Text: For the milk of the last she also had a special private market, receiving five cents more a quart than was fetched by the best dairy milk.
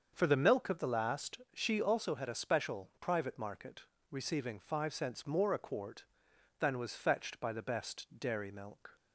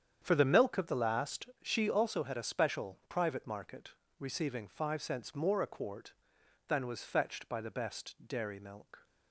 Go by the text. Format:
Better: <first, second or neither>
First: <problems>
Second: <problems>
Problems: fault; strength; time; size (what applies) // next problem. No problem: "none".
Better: first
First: starts louder than the rest; until 1.1 s; 6.5 dB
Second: gets quieter; strong; throughout; 12.5 dB // starts louder than the rest; strong; until 1.2 s; 8.5 dB